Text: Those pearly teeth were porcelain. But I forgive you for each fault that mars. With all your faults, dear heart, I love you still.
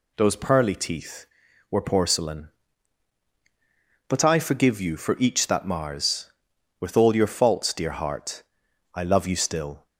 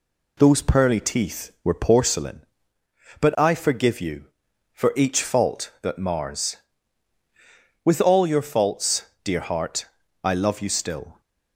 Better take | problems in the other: second | skips "fault"; at 5.4 s

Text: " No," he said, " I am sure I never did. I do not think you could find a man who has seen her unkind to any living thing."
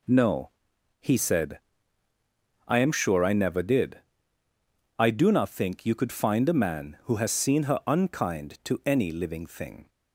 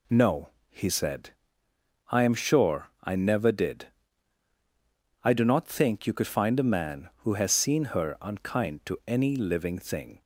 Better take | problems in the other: neither | none

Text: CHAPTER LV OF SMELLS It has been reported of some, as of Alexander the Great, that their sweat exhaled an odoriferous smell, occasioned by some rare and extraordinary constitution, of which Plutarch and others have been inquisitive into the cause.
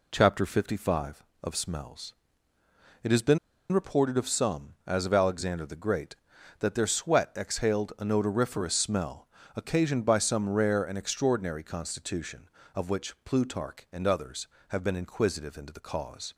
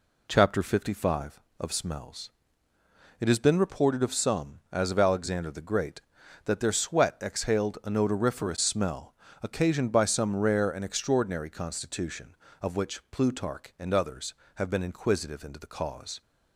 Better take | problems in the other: second | pauses between "SMELLS" and "It"; noticeable; at 2.1 s; 0.86 s long; noticeable in the second // pauses between "been" and "reported"; slight; at 3.3 s; 0.33 s long

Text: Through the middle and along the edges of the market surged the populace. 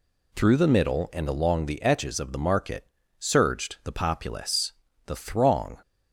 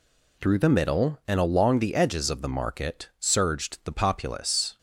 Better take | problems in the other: second | pauses between "market" and "surged"; slight; at 2.8 s; 0.32 s long // goes on to say "The throng"; noticeable; from 5.0 s on; 0.72 s long

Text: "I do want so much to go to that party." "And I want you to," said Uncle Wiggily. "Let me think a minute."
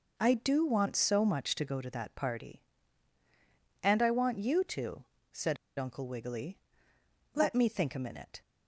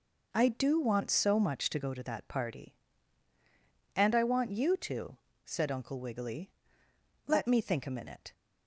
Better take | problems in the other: second | pauses between "said" and "Uncle"; slight; at 5.5 s; 0.22 s long

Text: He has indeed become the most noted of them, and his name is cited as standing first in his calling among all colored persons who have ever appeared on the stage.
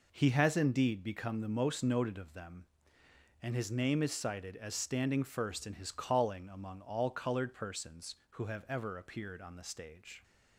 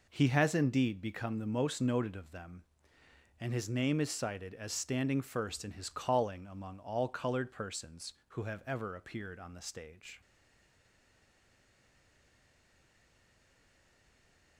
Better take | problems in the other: first | stays silent after the last word; strong; from 10.2 s on; 4.3 s long

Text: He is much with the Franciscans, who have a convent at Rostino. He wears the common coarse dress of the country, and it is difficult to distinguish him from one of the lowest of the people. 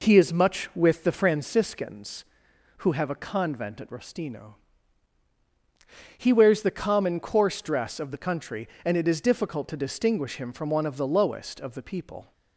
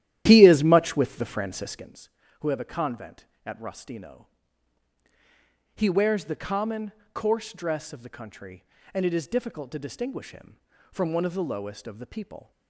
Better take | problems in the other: first | starts louder than the rest; strong; until 2.0 s; 12 dB // pauses between "common" and "coarse"; slight; at 6.9 s; 0.22 s long

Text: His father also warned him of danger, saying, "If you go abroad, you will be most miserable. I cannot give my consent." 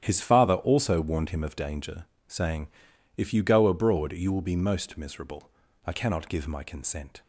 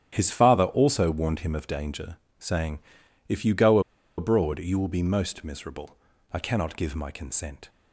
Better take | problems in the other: first | starts louder than the rest; strong; until 1.1 s; 10 dB; strong in the first // pauses between "go" and "abroad"; at 3.7 s; 0.38 s long

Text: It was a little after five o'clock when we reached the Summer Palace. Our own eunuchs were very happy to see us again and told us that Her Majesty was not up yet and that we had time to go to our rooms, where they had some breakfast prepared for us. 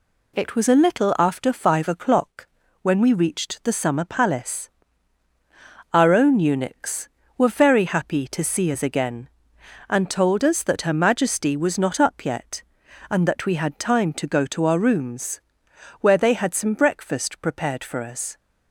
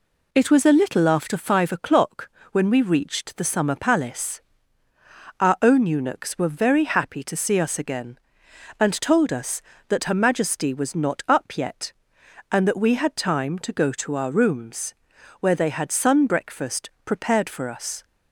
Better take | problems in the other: first | pauses between "o'clock" and "when"; slight; at 2.2 s; 0.24 s long; slight in the first // says "sun" for "some"; at 15.9 s // pauses between "breakfast" and "prepared"; slight; at 16.8 s; 0.16 s long

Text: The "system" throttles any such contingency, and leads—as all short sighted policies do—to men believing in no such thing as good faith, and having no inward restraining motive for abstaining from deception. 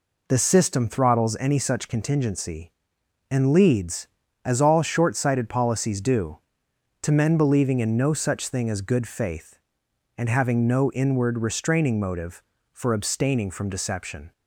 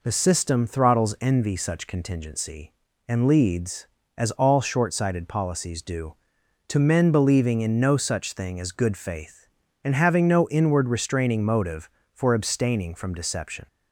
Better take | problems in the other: first | says "envy" for "any"; at 1.2 s

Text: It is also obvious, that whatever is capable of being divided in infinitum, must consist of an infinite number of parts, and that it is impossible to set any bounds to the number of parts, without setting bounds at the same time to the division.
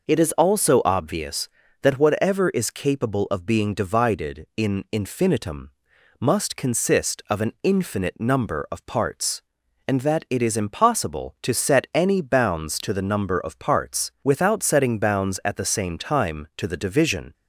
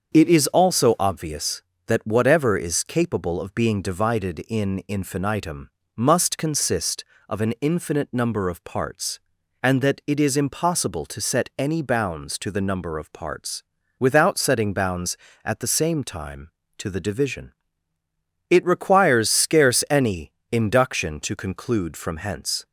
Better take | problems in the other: first | starts louder than the rest; until 1.2 s; 7 dB // goes on to say "It requires scarce any induction to conclude from hence"; strong; from 18.4 s on; 4.1 s long

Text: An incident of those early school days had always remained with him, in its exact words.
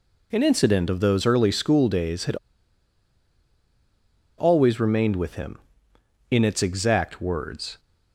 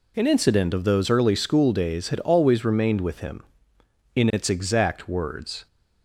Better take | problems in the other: second | pauses between "had" and "always"; strong; at 2.3 s; 2.0 s long

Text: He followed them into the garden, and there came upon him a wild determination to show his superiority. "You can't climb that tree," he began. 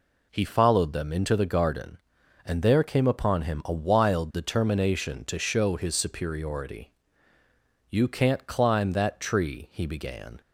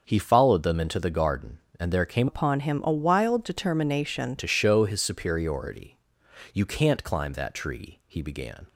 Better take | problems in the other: first | starts louder than the rest; until 1.0 s; 6 dB // changes voice from "upon" to "determination"; from 2.2 to 4.3 s; 2.1 s long

